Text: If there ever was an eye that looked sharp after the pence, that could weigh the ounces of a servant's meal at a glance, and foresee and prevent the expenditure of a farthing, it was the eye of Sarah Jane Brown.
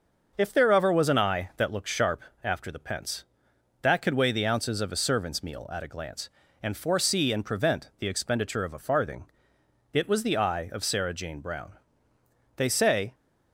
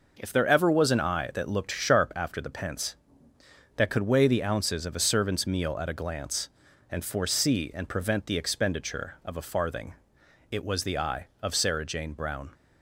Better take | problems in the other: second | starts louder than the rest; until 1.3 s; 6 dB // pauses between "sharp" and "after"; slight; at 2.1 s; 0.22 s long // goes on to say "They say"; from 12.5 s on; 0.58 s long

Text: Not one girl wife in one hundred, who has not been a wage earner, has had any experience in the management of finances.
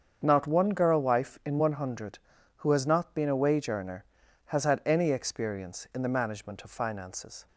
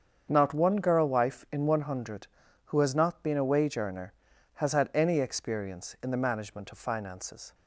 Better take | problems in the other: neither | starts louder than the rest; strong; the same in both

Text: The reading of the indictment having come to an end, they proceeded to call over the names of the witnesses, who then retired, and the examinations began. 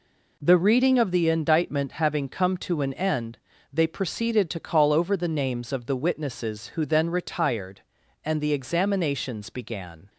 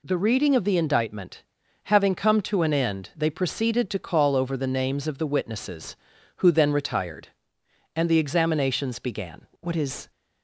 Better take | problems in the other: first | pauses between "indictment" and "having"; at 1.4 s; 0.42 s long // goes on to say "What is"; slight; from 9.6 s on; 0.48 s long

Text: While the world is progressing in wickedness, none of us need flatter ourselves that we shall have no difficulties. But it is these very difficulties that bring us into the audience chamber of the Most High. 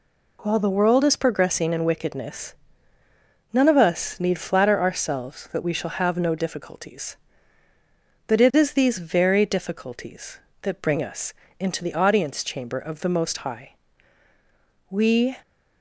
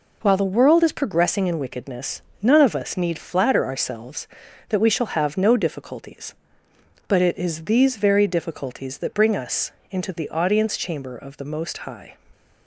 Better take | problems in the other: second | pauses between "us" and "into"; slight; at 11.3 s; 0.28 s long; slight in the second // goes on to say "We"; slight; from 14.8 s on; 0.48 s long

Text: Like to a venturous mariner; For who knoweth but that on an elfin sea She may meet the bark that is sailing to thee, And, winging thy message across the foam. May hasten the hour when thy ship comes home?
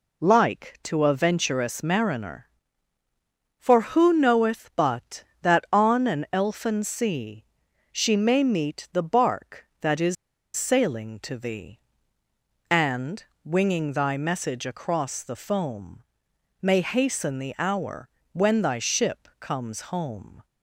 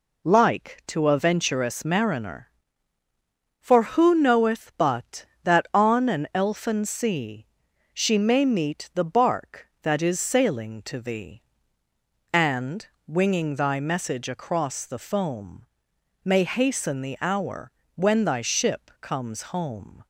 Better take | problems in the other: second | pauses between "sea" and "She"; noticeable; at 7.4 s; 0.48 s long; noticeable in the second // pauses between "is" and "sailing"; at 10.1 s; 0.41 s long // pauses between "hour" and "when"; slight; at 18.0 s; 0.26 s long; slight in the second

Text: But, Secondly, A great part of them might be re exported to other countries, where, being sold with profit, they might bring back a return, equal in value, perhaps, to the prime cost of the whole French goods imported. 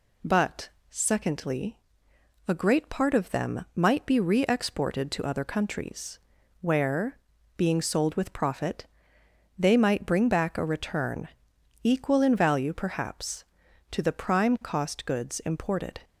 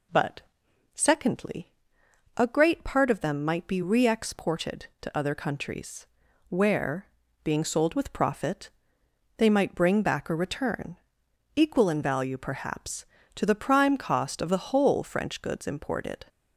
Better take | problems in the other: second | skips "of the whole French"; at 15.0 s

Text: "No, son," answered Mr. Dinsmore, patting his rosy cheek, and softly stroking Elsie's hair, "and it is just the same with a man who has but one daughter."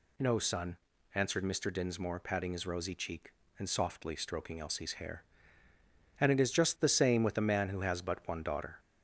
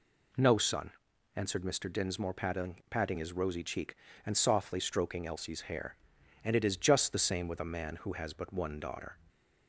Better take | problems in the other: first | says "patting" twice; at 2.8 s

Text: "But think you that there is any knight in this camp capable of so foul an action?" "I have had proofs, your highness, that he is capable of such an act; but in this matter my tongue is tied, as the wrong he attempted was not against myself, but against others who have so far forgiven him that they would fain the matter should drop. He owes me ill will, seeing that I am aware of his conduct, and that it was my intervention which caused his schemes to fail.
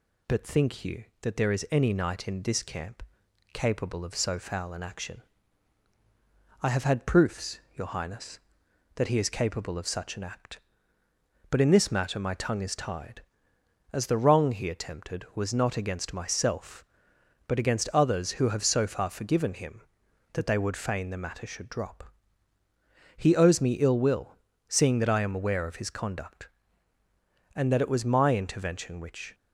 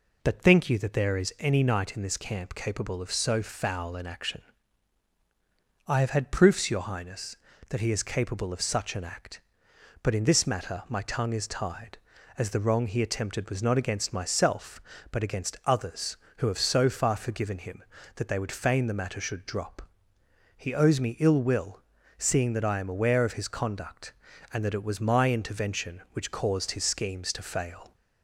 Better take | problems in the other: second | pauses between "camp" and "capable"; noticeable; at 3.0 s; 0.50 s long // stops before "caused his schemes to fail"; at 29.3 s

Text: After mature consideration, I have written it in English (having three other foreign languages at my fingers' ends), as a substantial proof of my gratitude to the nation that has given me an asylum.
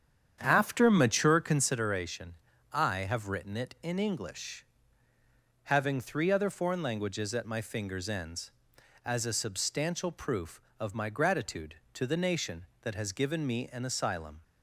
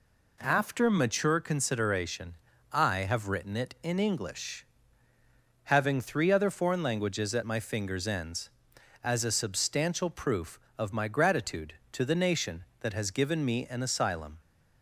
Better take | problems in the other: second | starts louder than the rest; strong; until 1.8 s; 8.5 dB

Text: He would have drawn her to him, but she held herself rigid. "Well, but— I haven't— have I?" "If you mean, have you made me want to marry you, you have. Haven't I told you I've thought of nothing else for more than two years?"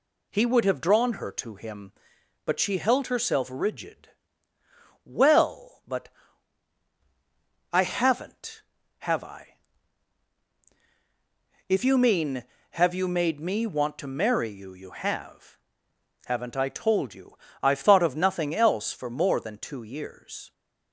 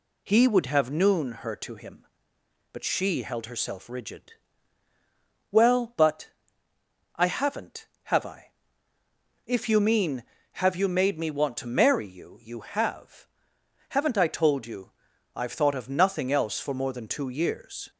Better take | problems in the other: first | says "noon" for "drawn"; at 0.9 s // pauses between "you" and "I've"; at 14.9 s; 0.44 s long; slight in the first

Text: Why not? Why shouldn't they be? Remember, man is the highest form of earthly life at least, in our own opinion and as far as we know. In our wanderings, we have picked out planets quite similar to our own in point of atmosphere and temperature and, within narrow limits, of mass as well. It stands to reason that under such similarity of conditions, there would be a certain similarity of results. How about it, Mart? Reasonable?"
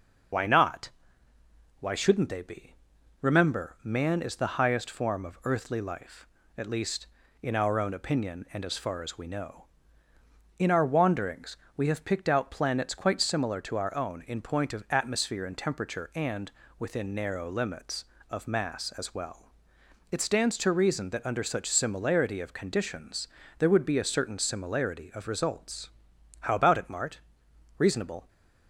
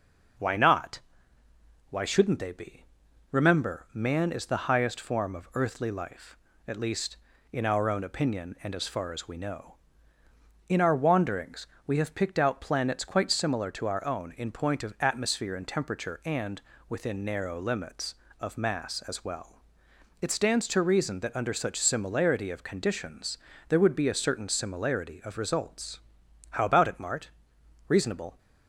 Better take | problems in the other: second | loses the start of "Why"; at 0.3 s; 50 ms // starts louder than the rest; noticeable; until 2.2 s; 6 dB; noticeable in the second

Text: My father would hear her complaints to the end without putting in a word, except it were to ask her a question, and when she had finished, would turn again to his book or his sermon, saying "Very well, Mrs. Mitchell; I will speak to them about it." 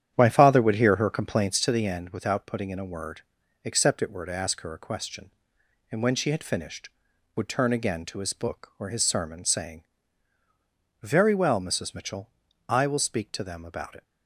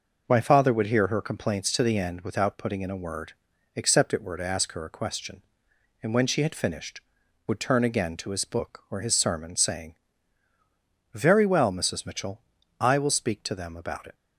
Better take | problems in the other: second | starts louder than the rest; strong; until 1.7 s; 9.5 dB // pauses between "saying" and "Very"; at 9.8 s; 1.1 s long; also in the second

